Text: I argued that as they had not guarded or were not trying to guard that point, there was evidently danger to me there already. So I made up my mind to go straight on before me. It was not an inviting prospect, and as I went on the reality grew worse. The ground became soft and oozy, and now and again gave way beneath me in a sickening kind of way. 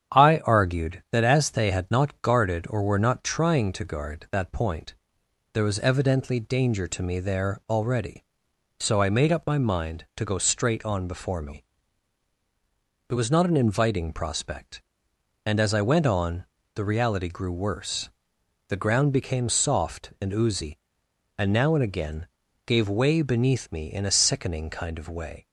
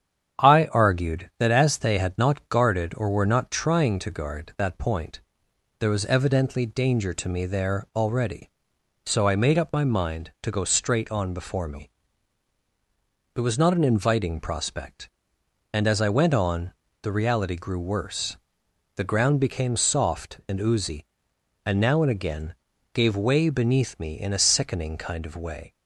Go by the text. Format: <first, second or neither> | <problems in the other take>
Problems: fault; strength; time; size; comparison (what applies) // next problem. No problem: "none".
neither | starts louder than the rest; strong; the same in both // pauses between "on" and "the"; slight; the same in both // pauses between "again" and "gave"; the same in both